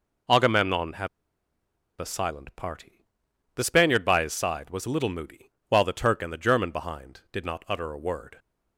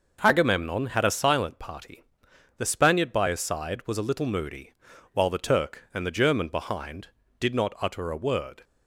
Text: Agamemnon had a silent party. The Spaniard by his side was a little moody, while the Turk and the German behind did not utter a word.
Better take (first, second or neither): second